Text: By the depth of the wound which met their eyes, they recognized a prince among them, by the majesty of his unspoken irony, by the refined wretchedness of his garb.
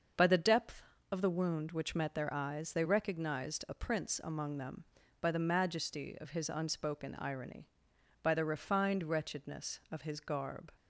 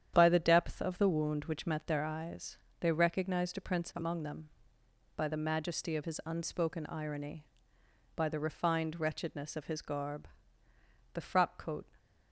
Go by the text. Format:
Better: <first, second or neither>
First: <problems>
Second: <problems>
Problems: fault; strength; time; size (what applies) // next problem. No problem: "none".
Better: first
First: starts louder than the rest; until 1.4 s; 6.5 dB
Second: starts louder than the rest; strong; until 1.1 s; 9.5 dB // goes on to say "The frock coat"; noticeable; from 11.1 s on; 0.84 s long